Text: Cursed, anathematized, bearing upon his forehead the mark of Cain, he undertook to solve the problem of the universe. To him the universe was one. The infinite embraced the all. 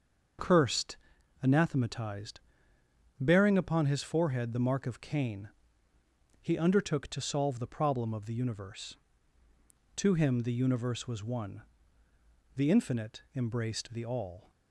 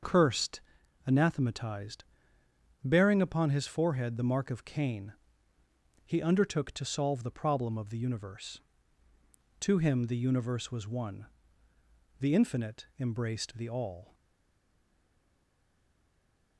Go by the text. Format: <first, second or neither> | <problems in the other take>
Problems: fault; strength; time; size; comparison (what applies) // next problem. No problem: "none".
first | starts louder than the rest; until 1.5 s; 6.5 dB; also in the first // stays silent after the last word; from 14.1 s on; 2.4 s long